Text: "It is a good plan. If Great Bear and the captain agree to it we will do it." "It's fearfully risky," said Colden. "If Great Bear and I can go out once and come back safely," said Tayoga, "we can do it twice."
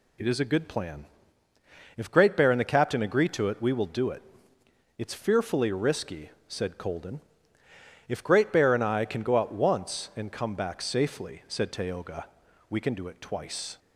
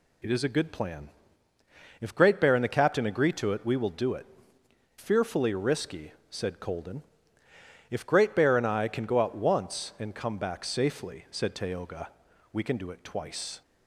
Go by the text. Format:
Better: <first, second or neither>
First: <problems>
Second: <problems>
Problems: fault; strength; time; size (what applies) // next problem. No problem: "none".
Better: first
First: none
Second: skips "It's"; at 4.6 s